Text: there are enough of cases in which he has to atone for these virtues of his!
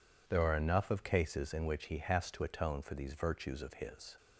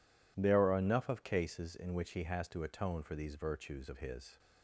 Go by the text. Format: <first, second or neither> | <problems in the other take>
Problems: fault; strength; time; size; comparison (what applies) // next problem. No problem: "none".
neither | none